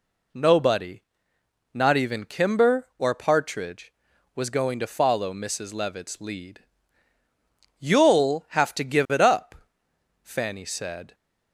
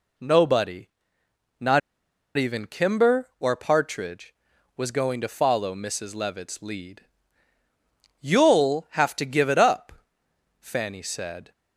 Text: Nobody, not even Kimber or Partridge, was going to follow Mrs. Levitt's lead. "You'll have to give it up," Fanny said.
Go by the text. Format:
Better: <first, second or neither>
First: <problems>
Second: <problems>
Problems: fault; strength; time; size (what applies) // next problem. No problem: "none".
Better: first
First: none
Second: pauses between "not" and "even"; noticeable; at 1.8 s; 0.57 s long